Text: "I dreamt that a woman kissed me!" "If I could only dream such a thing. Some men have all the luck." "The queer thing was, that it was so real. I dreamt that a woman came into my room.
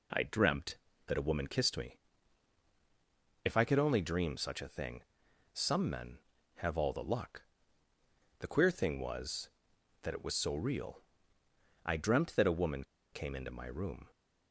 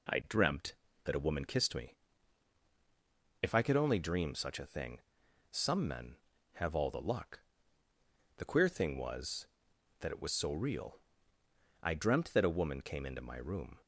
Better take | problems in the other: second | pauses between "woman" and "came"; slight; at 12.8 s; 0.29 s long

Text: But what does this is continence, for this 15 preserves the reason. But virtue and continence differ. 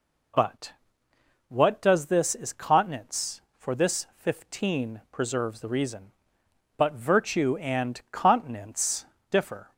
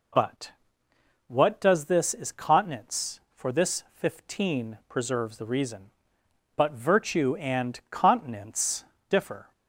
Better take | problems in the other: neither | pauses between "But" and "what"; noticeable; the same in both // pauses between "continence" and "differ"; slight; the same in both

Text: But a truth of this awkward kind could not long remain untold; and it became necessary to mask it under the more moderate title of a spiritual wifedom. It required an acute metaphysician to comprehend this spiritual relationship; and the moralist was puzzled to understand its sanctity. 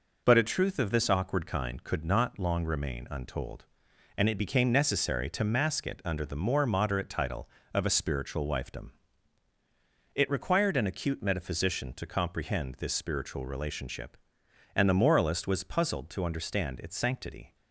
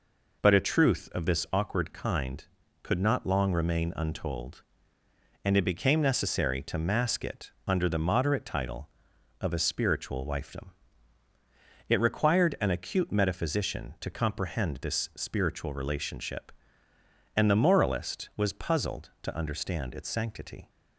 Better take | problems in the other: first | pauses between "it" and "under"; slight; at 7.5 s; 0.16 s long // skips "more"; at 7.9 s

